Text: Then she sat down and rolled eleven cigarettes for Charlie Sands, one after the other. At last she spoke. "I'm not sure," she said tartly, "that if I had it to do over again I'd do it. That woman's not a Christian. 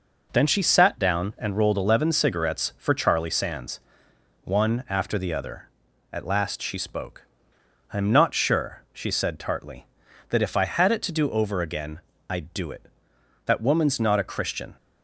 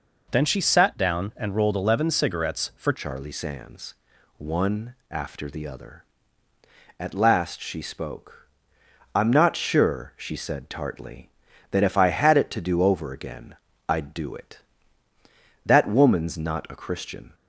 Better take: first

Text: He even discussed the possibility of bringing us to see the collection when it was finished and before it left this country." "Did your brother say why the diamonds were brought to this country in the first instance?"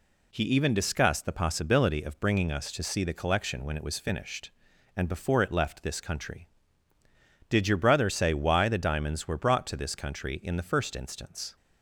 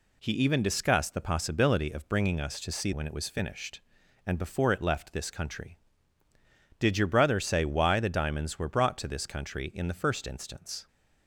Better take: first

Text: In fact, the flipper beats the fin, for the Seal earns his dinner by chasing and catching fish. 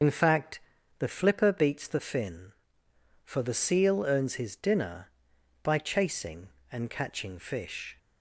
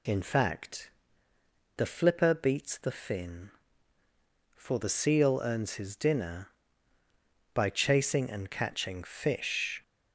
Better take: second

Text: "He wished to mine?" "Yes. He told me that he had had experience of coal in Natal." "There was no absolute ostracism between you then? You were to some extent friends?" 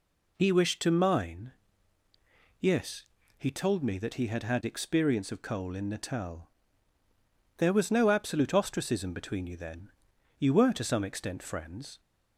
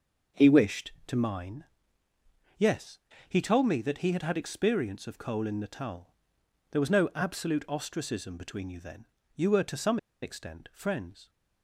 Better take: first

